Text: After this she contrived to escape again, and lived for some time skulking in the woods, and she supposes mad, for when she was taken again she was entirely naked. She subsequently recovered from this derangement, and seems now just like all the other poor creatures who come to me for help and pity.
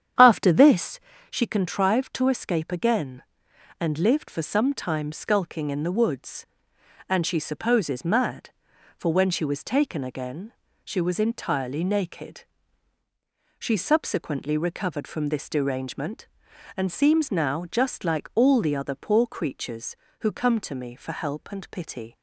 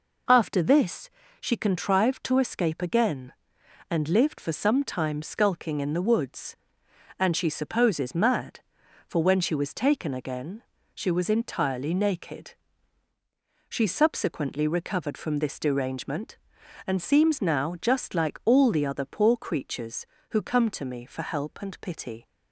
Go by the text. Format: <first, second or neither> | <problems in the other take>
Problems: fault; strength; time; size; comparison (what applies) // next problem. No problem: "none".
second | starts louder than the rest; strong; until 1.5 s; 9 dB // pauses between "this" and "she"; slight; at 0.9 s; 0.32 s long; slight in the second // pauses between "again" and "she"; slight; at 10.5 s; 0.32 s long; slight in the second